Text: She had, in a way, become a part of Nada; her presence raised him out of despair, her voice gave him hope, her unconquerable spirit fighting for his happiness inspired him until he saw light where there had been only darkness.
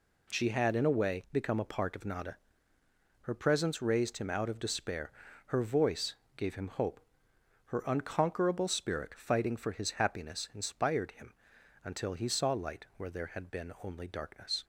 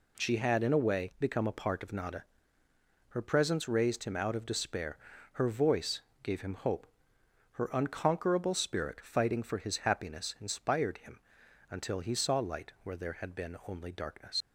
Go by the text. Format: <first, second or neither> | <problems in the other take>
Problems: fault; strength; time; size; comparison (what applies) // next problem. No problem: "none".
first | pauses between "voice" and "gave"; slight; at 5.9 s; 0.22 s long; slight in the first // pauses between "him" and "until"; noticeable; at 11.1 s; 0.50 s long; noticeable in the first // leaves "darkness" unfinished; at 14.4 s; 75 ms